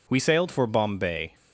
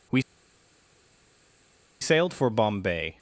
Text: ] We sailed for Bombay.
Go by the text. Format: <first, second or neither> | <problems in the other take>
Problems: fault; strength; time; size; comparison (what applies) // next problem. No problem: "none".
first | pauses between "We" and "sailed"; strong; at 0.2 s; 1.7 s long